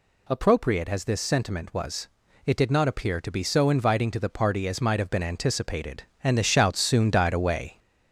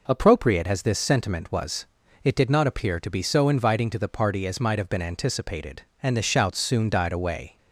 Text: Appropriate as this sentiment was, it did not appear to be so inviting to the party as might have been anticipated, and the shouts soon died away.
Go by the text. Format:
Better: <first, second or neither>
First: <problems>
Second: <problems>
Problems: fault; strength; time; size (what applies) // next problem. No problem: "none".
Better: second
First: gets louder; noticeable; throughout; 4.5 dB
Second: none